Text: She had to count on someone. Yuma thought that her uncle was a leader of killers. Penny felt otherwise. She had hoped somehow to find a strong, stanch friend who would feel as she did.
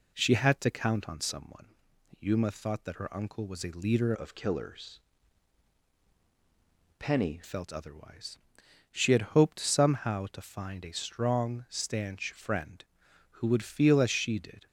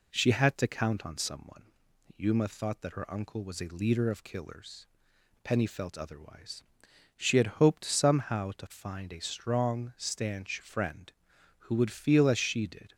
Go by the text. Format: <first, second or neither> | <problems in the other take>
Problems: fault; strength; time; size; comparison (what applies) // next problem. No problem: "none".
second | changes voice from "of" to "Penny"; from 4.1 to 7.3 s; 3.2 s long